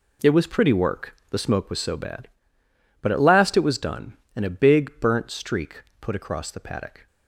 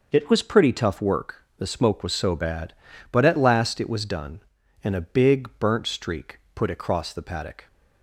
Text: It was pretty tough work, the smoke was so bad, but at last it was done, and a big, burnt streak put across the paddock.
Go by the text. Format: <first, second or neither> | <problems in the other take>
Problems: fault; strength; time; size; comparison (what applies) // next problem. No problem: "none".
second | skips "tough"; at 0.7 s // pauses between "streak" and "put"; slight; at 5.8 s; 0.20 s long; slight in the second